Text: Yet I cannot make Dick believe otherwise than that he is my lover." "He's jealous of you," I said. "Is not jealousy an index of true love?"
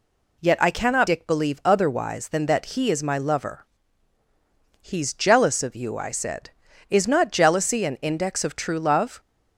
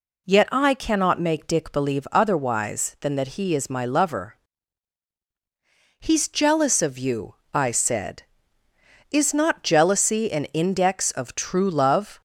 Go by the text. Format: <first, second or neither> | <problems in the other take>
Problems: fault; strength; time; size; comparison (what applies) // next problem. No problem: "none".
second | skips "make"; at 1.0 s